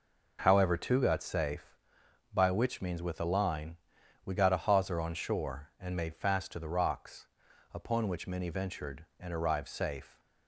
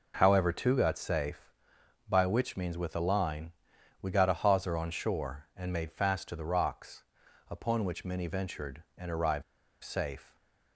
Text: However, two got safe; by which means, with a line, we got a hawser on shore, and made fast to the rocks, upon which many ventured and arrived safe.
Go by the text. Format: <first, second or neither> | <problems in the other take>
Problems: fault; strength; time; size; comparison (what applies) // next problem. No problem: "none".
first | pauses between "arrived" and "safe"; at 9.4 s; 0.40 s long